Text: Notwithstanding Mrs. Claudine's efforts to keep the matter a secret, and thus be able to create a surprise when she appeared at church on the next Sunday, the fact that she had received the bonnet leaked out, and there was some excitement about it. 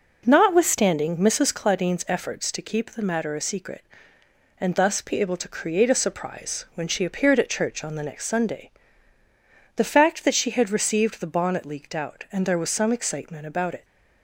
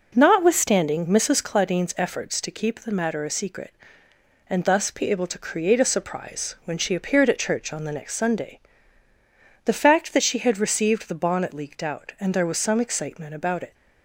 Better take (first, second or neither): neither